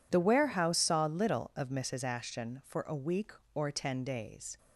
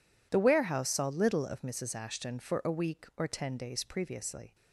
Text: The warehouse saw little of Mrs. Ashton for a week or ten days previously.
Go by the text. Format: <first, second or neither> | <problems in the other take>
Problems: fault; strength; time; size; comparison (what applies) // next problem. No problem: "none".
second | stops before "previously"; at 4.5 s